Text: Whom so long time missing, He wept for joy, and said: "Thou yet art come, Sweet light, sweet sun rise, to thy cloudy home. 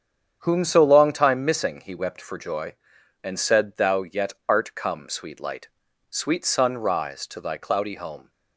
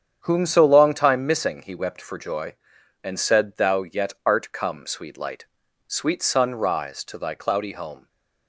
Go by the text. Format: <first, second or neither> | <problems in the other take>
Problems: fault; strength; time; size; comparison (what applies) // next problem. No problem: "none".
neither | starts louder than the rest; strong; the same in both